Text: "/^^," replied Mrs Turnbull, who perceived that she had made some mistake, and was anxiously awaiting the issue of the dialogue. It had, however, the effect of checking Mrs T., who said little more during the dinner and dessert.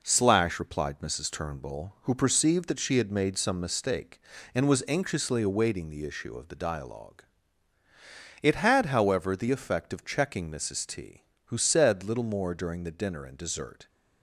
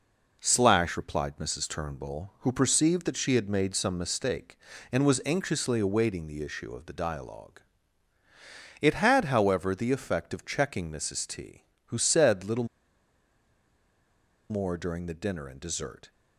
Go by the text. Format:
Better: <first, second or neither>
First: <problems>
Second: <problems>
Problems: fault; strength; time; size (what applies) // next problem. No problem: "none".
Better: first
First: none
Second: pauses between "little" and "more"; strong; at 12.6 s; 1.8 s long